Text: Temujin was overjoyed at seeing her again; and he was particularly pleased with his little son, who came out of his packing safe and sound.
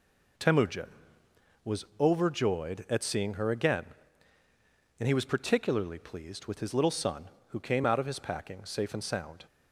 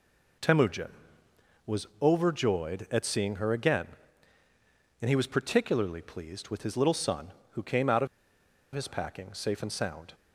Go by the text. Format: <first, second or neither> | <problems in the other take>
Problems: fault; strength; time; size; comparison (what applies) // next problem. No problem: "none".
first | pauses between "was" and "overjoyed"; slight; at 1.8 s; 0.16 s long; slight in the first // pauses between "of" and "his"; noticeable; at 8.0 s; 0.67 s long